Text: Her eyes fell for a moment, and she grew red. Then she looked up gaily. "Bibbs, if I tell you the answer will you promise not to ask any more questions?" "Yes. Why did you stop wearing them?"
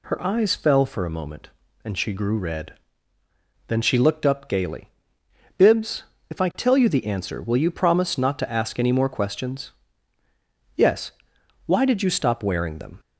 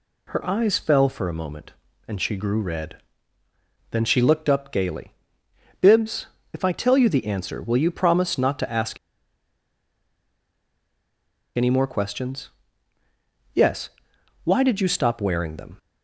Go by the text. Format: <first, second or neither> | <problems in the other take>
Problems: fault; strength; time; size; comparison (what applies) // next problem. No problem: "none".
first | pauses between "ask" and "any"; strong; at 8.9 s; 2.6 s long